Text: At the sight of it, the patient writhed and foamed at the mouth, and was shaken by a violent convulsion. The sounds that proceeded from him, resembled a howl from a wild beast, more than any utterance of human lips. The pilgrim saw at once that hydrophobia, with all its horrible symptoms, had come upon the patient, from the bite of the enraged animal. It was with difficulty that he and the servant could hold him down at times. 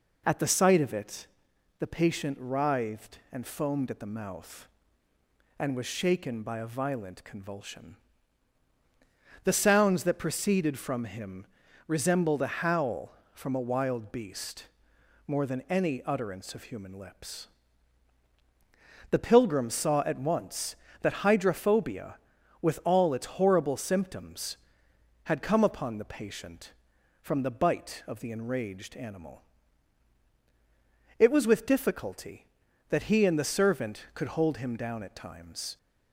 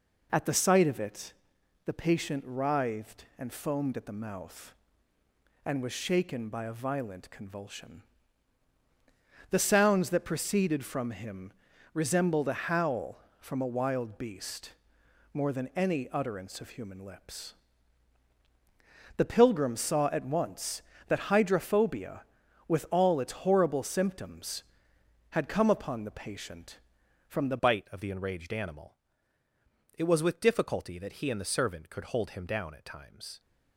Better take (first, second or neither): first